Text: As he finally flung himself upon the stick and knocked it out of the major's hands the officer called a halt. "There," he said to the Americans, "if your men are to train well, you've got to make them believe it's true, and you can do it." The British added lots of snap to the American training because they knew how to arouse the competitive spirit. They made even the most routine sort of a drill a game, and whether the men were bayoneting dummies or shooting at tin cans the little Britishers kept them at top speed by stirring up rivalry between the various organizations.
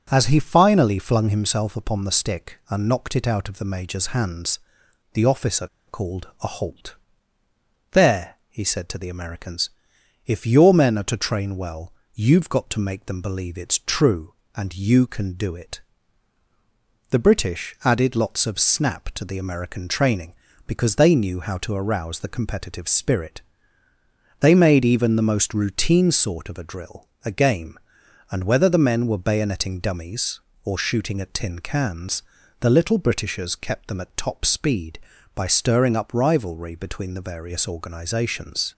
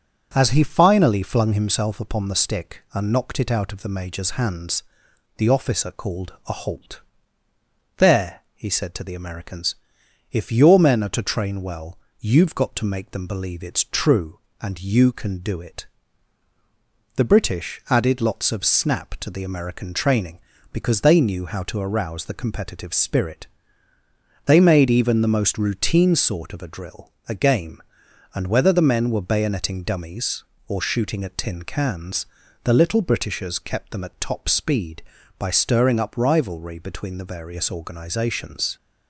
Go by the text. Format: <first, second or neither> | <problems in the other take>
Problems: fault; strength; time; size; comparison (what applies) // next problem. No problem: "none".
second | pauses between "hands" and "the"; noticeable; at 4.5 s; 0.54 s long; noticeable in the second // pauses between "officer" and "called"; slight; at 5.6 s; 0.21 s long // pauses between "drill" and "a"; slight; at 27.0 s; 0.18 s long; slight in the second // pauses between "cans" and "the"; at 32.2 s; 0.38 s long; also in the second